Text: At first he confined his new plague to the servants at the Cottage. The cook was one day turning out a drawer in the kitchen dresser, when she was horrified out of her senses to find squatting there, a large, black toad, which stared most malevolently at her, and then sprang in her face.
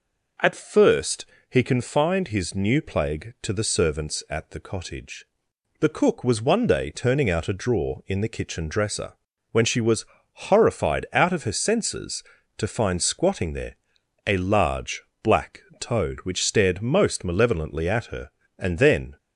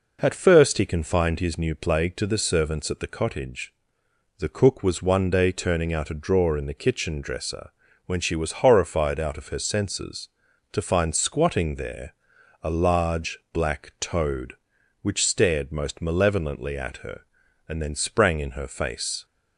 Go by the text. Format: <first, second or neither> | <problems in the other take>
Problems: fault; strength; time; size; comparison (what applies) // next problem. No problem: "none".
second | pauses between "first" and "he"; slight; at 1.2 s; 0.24 s long // pauses between "was" and "horrified"; slight; at 10.0 s; 0.28 s long // pauses between "black" and "toad"; slight; at 15.6 s; 0.18 s long // stops before "sprang in her face"; at 19.1 s